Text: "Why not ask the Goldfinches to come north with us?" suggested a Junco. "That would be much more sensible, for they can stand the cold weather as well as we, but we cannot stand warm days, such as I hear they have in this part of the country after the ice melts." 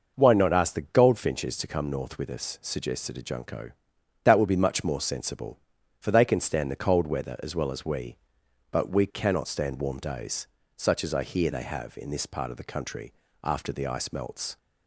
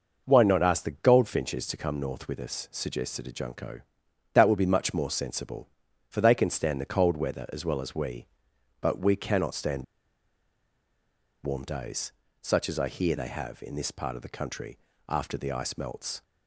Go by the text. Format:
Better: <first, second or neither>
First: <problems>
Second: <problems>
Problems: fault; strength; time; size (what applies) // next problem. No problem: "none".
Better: first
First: pauses between "country" and "after"; slight; at 13.1 s; 0.30 s long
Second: pauses between "stand" and "warm"; strong; at 9.8 s; 1.6 s long // pauses between "country" and "after"; slight; at 14.7 s; 0.30 s long